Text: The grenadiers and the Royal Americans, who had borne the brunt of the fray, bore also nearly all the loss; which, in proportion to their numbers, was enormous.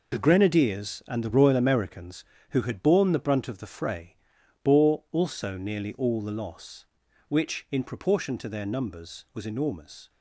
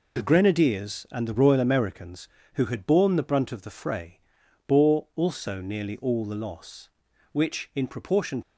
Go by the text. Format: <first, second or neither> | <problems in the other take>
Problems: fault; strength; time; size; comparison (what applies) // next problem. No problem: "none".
first | stops before "to their numbers was enormous"; at 8.4 s